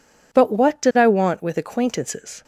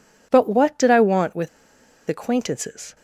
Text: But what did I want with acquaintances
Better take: first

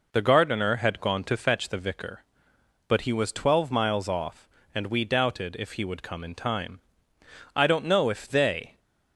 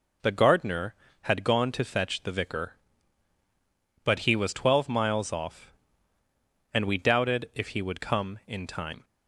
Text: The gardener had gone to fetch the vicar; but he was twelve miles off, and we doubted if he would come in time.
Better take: second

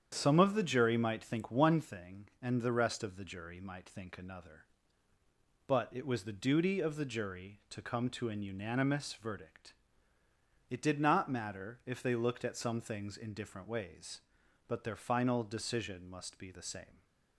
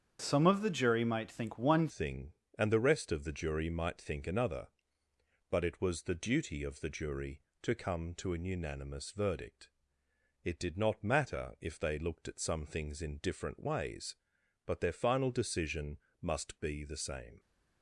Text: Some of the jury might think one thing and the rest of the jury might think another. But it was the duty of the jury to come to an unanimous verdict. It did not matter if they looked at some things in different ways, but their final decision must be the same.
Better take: first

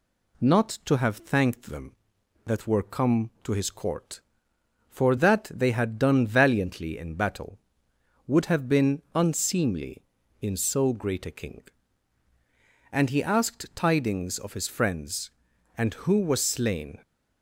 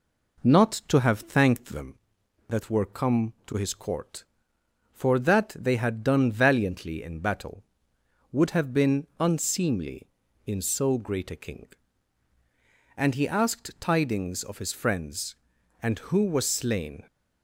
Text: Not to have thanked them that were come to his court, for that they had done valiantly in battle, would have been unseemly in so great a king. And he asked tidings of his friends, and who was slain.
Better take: first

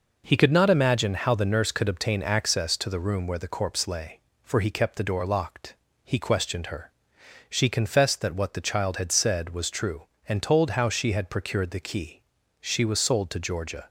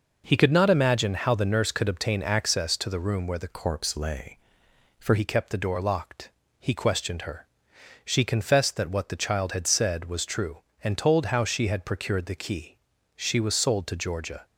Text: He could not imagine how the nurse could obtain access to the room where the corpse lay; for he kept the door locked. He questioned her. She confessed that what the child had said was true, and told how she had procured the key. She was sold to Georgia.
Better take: first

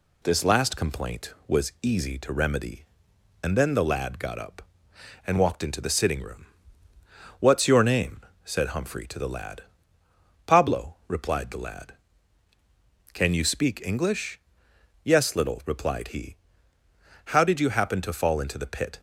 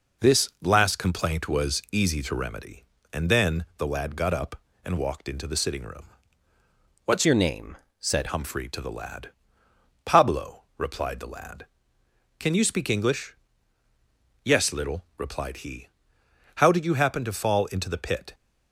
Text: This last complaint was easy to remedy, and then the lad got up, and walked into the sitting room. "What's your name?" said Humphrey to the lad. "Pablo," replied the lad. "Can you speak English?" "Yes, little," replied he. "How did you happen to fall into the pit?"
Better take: first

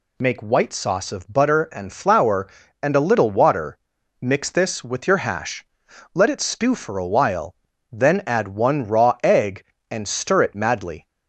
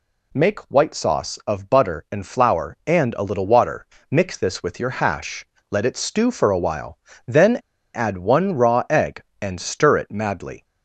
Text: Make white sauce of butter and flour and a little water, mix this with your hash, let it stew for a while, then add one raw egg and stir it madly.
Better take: first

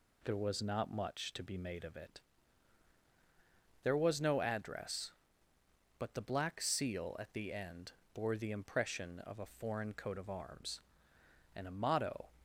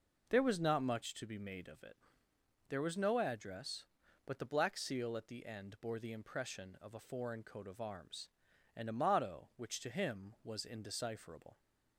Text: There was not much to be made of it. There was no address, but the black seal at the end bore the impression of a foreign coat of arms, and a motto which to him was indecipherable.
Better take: second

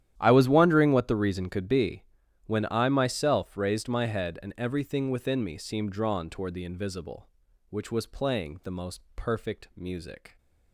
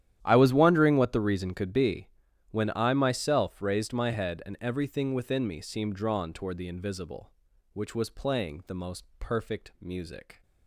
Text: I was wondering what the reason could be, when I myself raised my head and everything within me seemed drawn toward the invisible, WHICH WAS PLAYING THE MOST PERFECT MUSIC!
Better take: neither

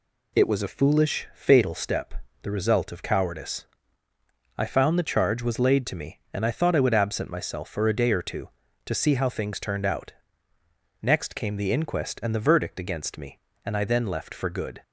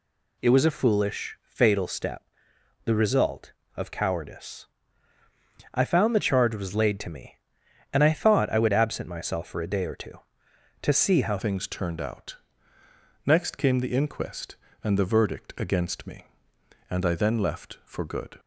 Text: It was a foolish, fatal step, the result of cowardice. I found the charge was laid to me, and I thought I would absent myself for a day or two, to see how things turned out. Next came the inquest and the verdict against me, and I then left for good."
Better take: first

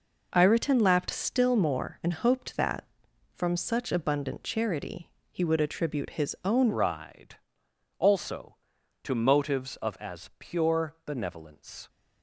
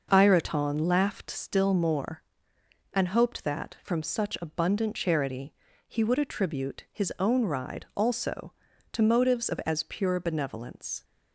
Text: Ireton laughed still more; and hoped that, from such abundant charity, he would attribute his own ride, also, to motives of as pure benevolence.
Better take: second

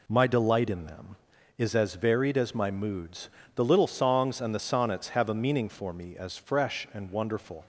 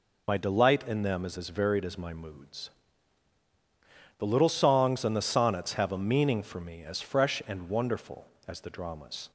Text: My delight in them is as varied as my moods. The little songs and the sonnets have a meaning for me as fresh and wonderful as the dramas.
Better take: second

